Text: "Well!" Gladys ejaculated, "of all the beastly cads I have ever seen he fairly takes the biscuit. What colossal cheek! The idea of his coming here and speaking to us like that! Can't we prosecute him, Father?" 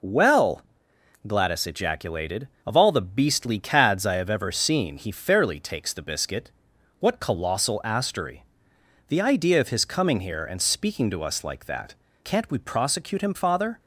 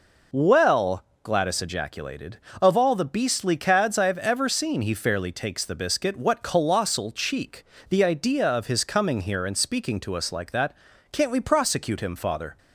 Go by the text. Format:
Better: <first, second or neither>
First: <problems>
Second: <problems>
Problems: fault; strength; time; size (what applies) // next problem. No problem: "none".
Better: second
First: says "astery" for "cheek"; at 7.8 s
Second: none